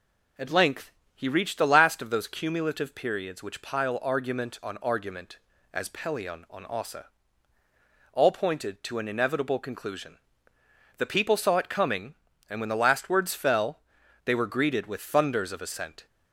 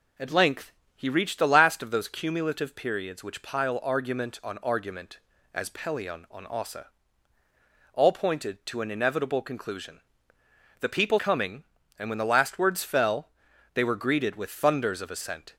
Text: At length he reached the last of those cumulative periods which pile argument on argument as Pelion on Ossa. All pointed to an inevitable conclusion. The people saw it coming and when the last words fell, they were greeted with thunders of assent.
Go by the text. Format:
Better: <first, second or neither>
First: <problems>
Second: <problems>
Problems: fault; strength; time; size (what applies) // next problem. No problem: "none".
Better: first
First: pauses between "length" and "he"; slight; at 0.9 s; 0.22 s long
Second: pauses between "length" and "he"; slight; at 0.7 s; 0.22 s long // skips "saw it"; at 11.1 s